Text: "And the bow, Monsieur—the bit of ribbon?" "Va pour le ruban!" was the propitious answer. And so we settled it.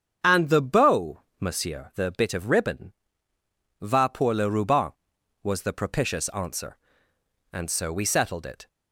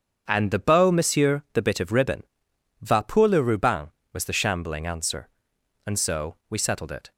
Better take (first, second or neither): first